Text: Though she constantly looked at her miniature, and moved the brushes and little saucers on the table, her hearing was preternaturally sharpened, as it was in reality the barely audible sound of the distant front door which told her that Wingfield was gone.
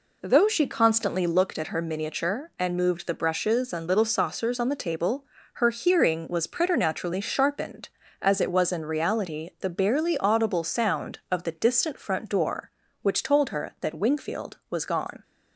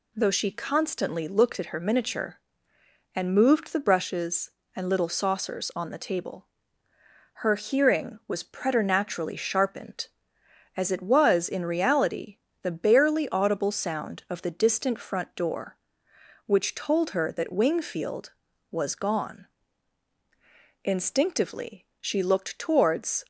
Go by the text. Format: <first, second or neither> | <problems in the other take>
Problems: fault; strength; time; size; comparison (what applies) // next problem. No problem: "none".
first | pauses between "reality" and "the"; slight; at 12.3 s; 0.26 s long // goes on to say "Instinctively she looked towards"; strong; from 20.8 s on; 2.4 s long